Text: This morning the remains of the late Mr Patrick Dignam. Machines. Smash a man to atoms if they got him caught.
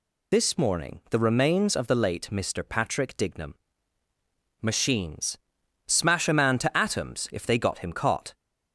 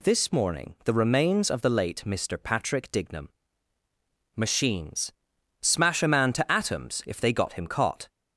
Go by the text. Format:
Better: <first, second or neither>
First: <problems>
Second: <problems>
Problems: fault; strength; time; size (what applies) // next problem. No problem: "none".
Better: second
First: loses the start of "This"; at 0.3 s; 60 ms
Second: none